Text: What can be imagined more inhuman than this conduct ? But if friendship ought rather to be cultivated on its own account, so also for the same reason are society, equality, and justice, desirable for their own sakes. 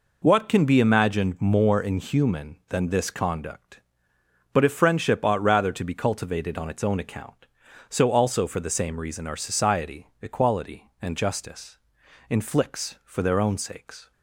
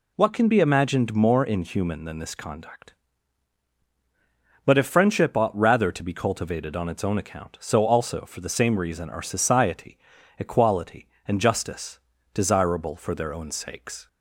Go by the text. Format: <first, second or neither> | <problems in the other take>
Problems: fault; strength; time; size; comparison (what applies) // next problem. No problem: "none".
second | says "inflicts" for "desirable"; at 12.2 s